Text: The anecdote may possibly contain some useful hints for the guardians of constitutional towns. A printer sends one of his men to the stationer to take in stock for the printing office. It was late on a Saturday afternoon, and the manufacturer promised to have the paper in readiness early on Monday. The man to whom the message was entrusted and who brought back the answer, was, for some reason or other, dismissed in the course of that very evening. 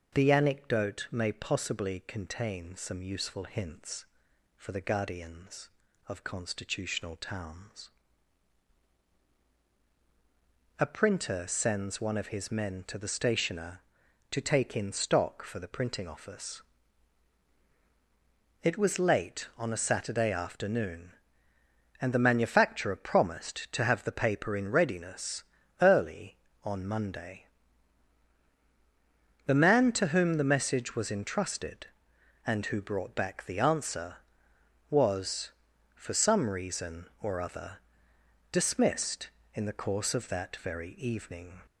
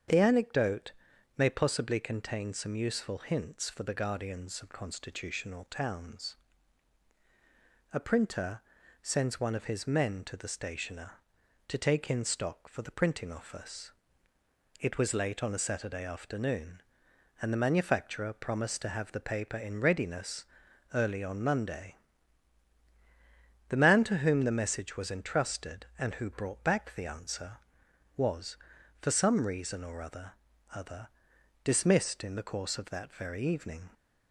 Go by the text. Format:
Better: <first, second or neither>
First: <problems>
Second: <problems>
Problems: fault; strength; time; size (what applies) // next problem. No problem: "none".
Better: first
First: starts louder than the rest; noticeable; until 1.1 s; 6 dB // pauses between "readiness" and "early"; at 25.4 s; 0.40 s long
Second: starts louder than the rest; strong; until 1.5 s; 7.5 dB // pauses between "anecdote" and "may"; noticeable; at 0.9 s; 0.46 s long // pauses between "printer" and "sends"; at 8.6 s; 0.42 s long // pauses between "readiness" and "early"; noticeable; at 20.4 s; 0.46 s long // says "other" twice; at 30.7 s